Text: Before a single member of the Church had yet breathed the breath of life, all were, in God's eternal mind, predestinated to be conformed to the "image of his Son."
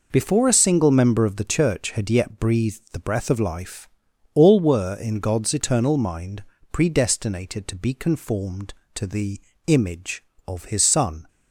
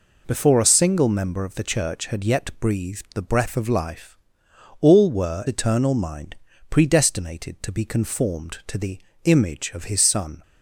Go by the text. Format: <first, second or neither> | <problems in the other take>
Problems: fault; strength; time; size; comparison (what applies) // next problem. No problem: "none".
first | skips "in God's"; at 5.4 s // pauses between "the" and "image"; slight; at 8.9 s; 0.28 s long; slight in the first